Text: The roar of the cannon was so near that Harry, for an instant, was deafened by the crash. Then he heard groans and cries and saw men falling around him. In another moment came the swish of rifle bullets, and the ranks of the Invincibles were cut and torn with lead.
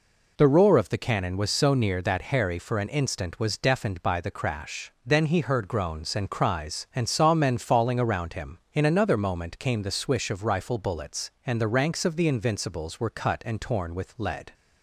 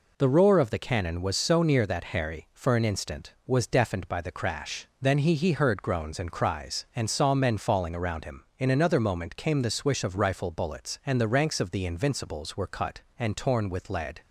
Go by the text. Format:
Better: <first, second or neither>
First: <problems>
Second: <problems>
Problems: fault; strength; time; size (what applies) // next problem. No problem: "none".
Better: first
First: none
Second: says "he" twice; at 5.3 s